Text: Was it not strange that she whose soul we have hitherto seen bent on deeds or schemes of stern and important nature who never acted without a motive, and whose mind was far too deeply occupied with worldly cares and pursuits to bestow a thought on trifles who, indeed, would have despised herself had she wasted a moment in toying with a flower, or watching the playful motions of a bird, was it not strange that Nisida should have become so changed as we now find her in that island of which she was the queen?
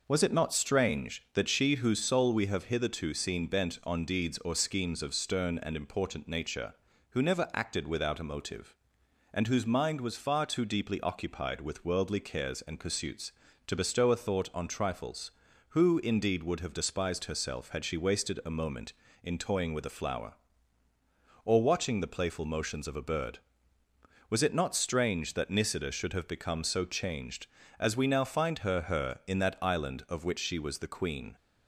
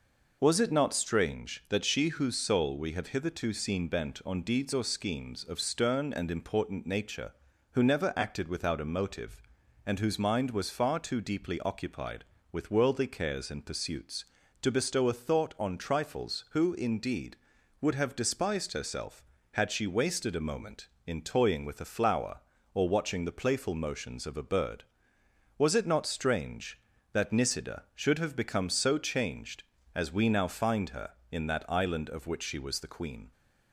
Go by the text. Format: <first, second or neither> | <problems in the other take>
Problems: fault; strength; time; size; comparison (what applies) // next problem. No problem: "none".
second | says "her" twice; at 28.8 s